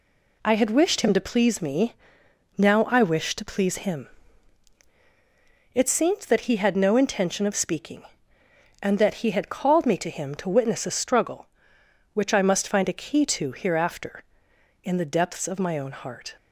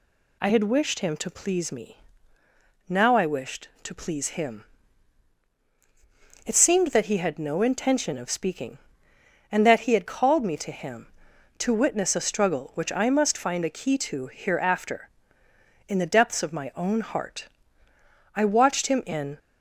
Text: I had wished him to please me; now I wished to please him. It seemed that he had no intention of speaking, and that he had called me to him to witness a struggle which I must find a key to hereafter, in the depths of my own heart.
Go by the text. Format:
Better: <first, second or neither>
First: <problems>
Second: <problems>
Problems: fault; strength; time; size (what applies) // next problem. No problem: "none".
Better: first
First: none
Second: goes on to say "I watched him in"; noticeable; from 18.3 s on; 1.0 s long